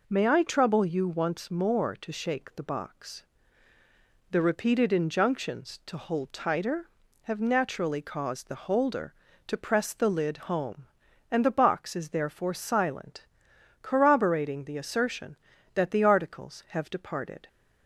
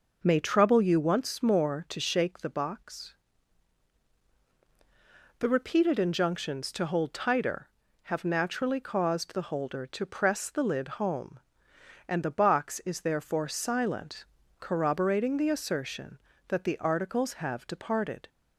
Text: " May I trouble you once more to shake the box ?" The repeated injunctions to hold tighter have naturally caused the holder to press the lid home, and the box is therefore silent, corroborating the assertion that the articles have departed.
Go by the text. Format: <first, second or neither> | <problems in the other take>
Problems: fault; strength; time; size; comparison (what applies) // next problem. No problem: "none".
first | starts louder than the rest; until 1.2 s; 6 dB // skips "I"; at 0.3 s // pauses between "lid" and "home"; slight; at 10.8 s; 0.16 s long